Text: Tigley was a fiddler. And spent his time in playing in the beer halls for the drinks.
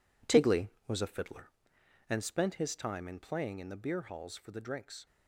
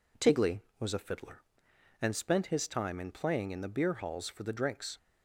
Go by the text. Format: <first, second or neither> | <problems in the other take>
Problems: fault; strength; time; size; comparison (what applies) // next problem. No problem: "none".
second | gets quieter; strong; throughout; 10 dB